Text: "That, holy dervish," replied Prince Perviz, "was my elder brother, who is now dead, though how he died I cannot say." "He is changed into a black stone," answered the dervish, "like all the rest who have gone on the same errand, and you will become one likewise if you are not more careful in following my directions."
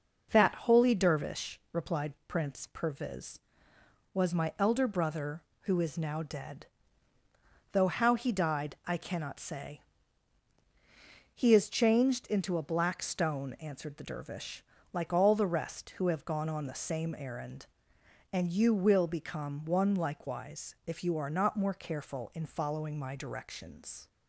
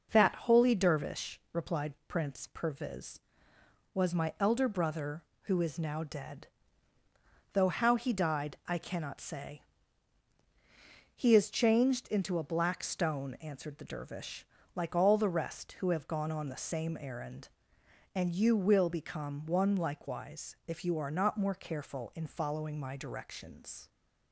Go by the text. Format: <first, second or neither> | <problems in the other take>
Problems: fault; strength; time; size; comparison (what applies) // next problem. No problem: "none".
neither | none